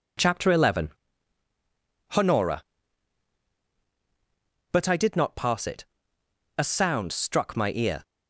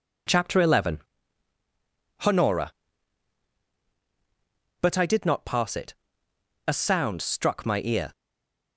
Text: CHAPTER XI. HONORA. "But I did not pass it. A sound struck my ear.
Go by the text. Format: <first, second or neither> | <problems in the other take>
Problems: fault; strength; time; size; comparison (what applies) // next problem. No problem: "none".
first | stays silent after the last word; slight; from 8.1 s on; 0.6 s long